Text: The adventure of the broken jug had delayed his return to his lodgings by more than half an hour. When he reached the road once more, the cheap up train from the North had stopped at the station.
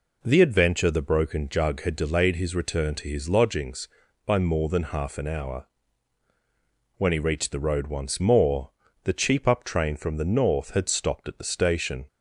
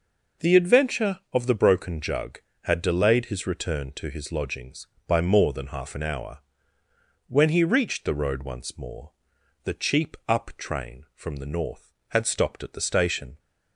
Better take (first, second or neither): second